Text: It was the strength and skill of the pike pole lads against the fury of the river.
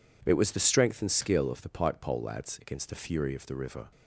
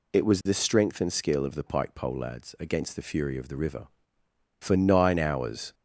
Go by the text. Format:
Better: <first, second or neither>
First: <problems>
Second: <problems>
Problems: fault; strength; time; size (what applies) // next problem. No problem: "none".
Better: first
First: none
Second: goes on to say "For nine hours"; noticeable; from 4.5 s on; 1.1 s long